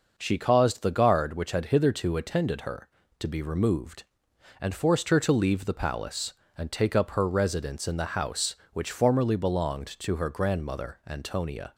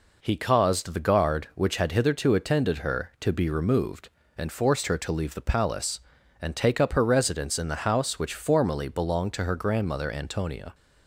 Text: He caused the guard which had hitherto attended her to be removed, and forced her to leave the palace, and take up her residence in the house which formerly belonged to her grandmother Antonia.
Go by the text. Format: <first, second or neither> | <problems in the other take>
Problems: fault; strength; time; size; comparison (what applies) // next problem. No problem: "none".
second | says "She" for "He"; at 0.1 s